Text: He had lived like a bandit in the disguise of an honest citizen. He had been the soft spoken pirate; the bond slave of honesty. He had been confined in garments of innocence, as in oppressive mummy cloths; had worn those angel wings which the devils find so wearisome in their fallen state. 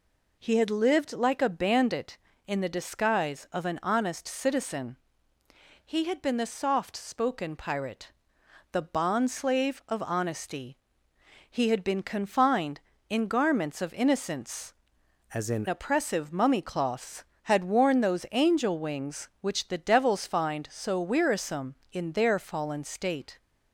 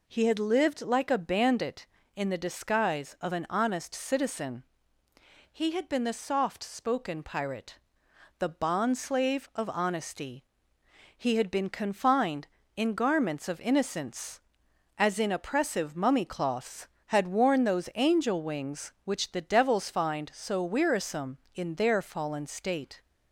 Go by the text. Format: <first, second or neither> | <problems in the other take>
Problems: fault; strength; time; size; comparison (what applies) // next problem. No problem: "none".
second | changes voice from "as" to "in"; from 15.3 to 15.6 s; 0.3 s long